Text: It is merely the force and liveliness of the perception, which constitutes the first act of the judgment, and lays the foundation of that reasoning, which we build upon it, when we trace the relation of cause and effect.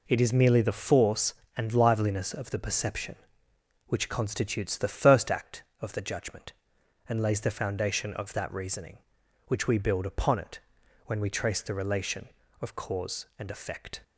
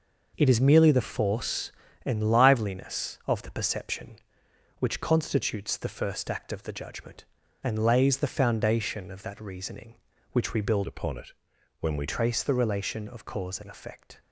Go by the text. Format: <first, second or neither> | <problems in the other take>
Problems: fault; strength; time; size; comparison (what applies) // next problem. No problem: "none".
first | changes voice from "upon" to "we"; from 10.8 to 12.0 s; 1.2 s long